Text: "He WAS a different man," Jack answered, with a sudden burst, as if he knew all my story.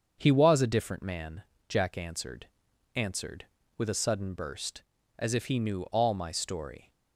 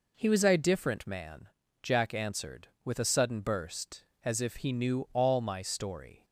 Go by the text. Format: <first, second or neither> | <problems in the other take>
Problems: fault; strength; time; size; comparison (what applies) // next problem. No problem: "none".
second | starts louder than the rest; until 1.2 s; 7 dB // says "answered" twice; at 2.9 s